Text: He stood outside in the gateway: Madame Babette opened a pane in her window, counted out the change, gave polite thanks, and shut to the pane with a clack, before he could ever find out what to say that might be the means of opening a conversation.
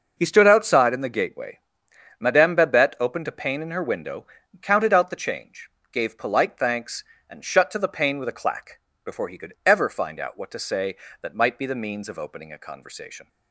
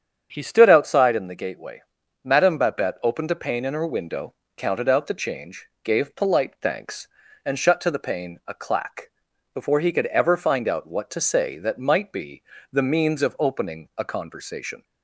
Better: first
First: none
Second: starts louder than the rest; strong; until 1.3 s; 8 dB // skips "with"; at 8.4 s // pauses between "be" and "the"; slight; at 12.4 s; 0.28 s long

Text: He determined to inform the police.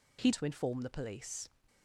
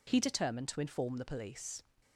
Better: second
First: skips "determined"; at 0.3 s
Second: none

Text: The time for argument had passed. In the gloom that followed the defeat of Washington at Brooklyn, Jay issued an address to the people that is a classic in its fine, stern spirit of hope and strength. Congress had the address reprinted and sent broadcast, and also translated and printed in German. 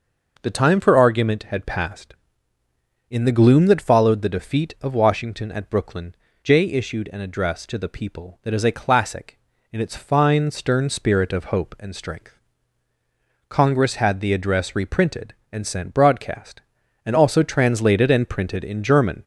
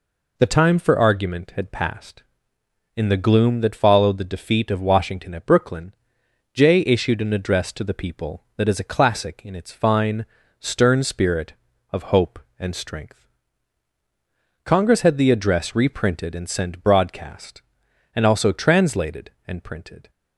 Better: first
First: none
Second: stops before "in German"; at 20.0 s

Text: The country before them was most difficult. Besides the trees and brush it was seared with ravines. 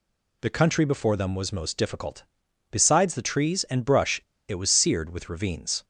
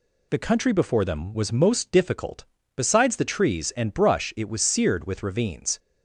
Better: second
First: pauses between "brush" and "it"; slight; at 4.2 s; 0.26 s long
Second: none

